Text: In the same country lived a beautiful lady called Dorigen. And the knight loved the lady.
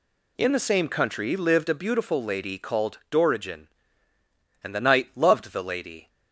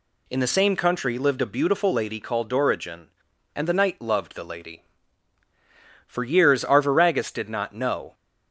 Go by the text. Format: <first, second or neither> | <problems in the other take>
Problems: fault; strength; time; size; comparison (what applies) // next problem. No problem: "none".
first | goes on to say "For years Arviragus did not know"; strong; from 6.0 s on; 2.0 s long